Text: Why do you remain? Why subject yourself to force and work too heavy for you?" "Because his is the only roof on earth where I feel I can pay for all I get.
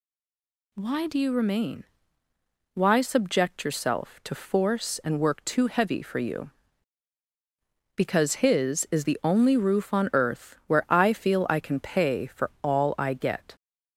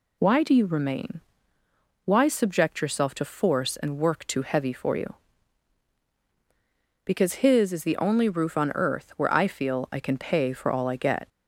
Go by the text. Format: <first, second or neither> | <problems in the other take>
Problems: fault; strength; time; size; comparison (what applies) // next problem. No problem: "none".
second | stays silent before the first word; slight; until 0.7 s; 0.7 s long